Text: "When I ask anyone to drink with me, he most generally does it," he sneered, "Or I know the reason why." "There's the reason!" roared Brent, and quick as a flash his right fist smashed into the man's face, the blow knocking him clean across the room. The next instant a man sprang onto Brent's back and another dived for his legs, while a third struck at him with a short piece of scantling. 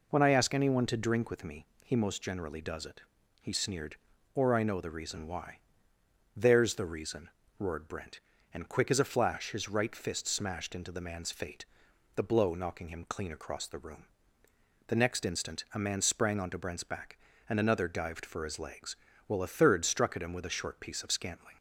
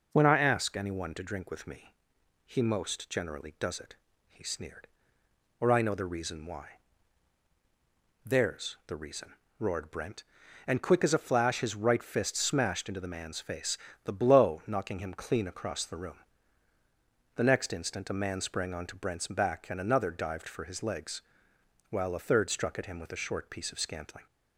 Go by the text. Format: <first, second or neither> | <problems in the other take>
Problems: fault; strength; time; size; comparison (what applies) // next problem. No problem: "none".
second | says "fate" for "face"; at 11.3 s